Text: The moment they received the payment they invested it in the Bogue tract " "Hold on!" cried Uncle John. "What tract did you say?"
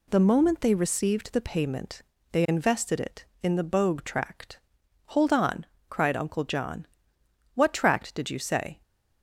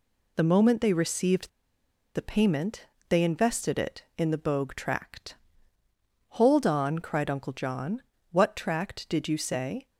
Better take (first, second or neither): first